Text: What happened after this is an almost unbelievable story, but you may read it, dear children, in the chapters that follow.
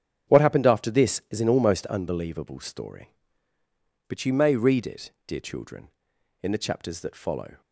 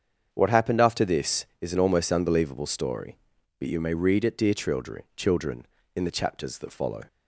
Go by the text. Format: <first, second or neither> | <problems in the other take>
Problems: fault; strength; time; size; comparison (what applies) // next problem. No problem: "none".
first | starts louder than the rest; strong; until 1.3 s; 7.5 dB; strong in the first // says "children" twice; at 5.1 s